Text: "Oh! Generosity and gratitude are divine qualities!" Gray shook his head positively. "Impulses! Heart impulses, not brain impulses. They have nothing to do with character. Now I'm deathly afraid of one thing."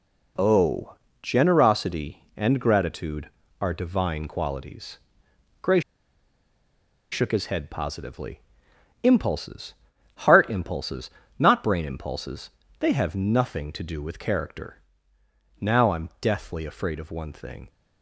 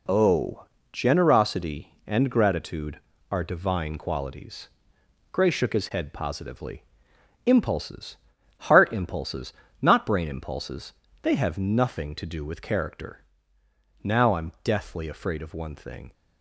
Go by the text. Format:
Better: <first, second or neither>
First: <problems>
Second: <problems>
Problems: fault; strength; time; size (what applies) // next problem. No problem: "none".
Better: second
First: pauses between "Gray" and "shook"; strong; at 5.8 s; 1.3 s long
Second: none